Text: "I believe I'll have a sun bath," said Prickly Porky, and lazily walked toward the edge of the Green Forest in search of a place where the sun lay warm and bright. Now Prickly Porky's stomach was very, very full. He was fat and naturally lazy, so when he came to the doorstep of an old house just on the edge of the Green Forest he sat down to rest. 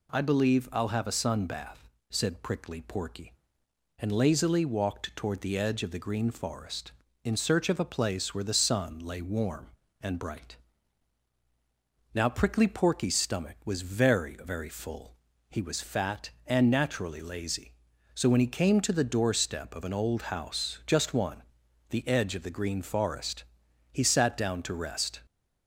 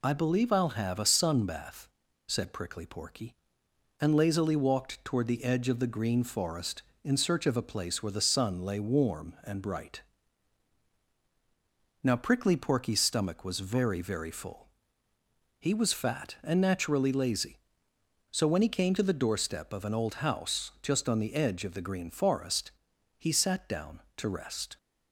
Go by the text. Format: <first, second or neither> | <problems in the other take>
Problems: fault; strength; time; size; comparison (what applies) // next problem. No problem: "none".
second | says "one" for "on"; at 21.1 s // pauses between "Forest" and "he"; noticeable; at 23.4 s; 0.48 s long; noticeable in the second